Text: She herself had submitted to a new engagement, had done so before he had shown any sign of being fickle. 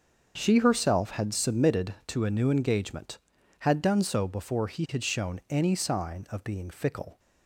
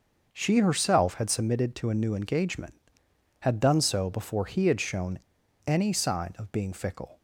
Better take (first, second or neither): first